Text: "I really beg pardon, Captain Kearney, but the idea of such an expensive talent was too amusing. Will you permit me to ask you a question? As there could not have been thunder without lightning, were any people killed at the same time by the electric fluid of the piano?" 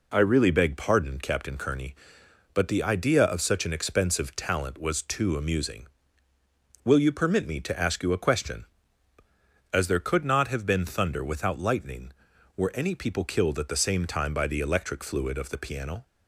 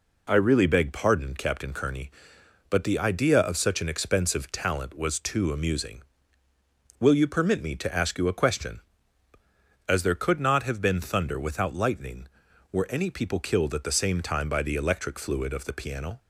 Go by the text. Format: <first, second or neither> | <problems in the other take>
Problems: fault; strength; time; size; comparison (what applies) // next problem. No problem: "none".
neither | none